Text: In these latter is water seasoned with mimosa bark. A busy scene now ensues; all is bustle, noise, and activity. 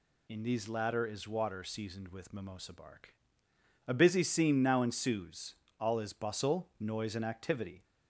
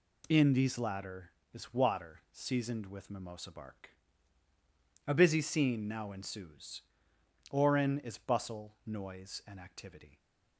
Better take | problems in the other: first | says "orin" for "all"; at 7.5 s

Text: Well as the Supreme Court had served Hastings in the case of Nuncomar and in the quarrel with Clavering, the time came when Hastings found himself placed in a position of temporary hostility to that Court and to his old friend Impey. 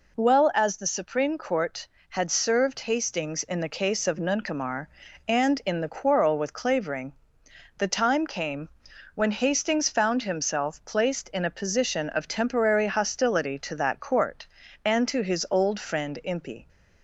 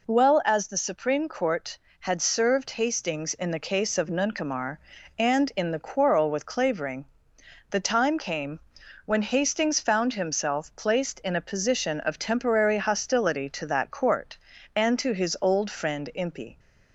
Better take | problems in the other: neither | pauses between "came" and "when"; noticeable; the same in both

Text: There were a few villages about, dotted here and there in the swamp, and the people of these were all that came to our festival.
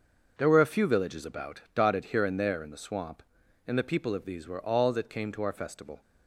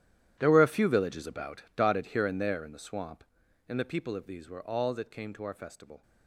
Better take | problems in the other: first | gets quieter; strong; throughout; 17.5 dB // starts louder than the rest; strong; until 1.4 s; 11.5 dB; also in the first

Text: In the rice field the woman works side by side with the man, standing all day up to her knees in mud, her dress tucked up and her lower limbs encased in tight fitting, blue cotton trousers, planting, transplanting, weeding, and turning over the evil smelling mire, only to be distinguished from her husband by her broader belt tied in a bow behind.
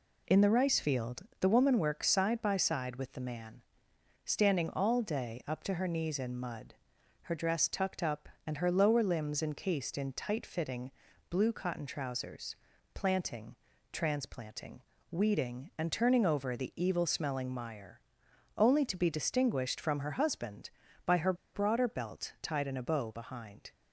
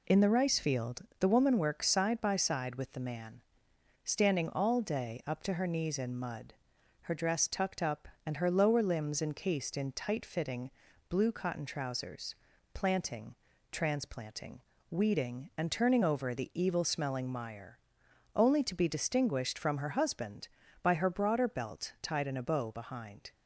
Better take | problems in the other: second | pauses between "field" and "the"; slight; at 1.2 s; 0.16 s long; slight in the second // pauses between "her" and "broader"; slight; at 21.3 s; 0.20 s long

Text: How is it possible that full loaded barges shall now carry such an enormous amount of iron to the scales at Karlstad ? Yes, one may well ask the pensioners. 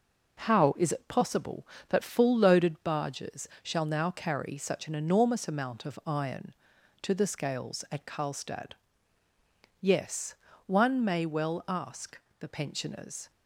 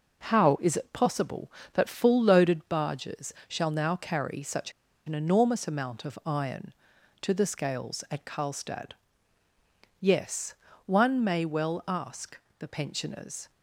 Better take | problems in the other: first | pauses between "such" and "an"; slight; at 4.7 s; 0.34 s long // pauses between "ask" and "the"; slight; at 12.3 s; 0.20 s long; slight in the first

